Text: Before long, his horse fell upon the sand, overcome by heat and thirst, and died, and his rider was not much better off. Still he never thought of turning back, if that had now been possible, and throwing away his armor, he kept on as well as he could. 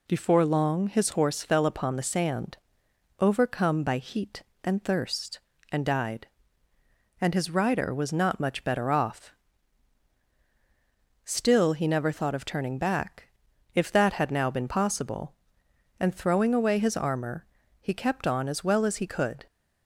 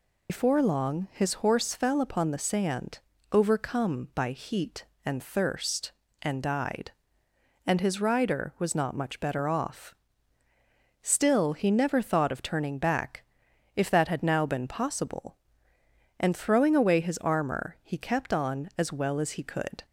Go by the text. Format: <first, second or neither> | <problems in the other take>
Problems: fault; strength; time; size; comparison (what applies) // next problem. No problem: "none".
first | loses the start of "Before"; at 0.2 s; 100 ms